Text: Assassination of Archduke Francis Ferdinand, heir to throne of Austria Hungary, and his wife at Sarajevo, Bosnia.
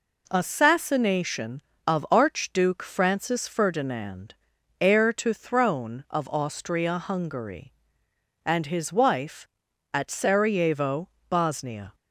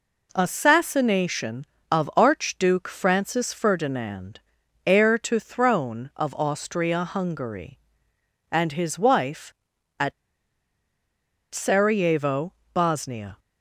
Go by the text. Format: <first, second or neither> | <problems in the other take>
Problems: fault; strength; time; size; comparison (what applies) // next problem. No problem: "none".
first | pauses between "at" and "Sarajevo"; strong; at 10.1 s; 1.3 s long